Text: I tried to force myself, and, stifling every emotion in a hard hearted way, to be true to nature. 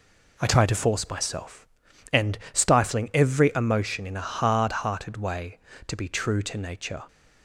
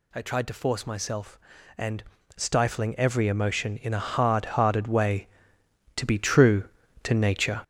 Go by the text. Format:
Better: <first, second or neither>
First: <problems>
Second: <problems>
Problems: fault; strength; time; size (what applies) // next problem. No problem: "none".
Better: first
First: none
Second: gets louder; strong; throughout; 9 dB